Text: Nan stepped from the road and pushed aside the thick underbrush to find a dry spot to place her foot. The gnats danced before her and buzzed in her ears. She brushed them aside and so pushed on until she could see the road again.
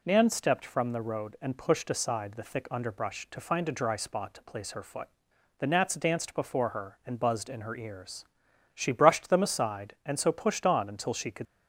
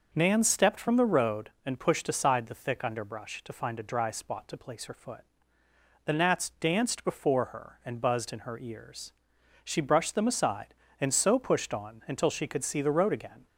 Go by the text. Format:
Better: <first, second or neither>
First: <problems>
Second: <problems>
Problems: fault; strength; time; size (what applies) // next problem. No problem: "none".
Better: second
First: stops before "see the road again"; at 11.4 s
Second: none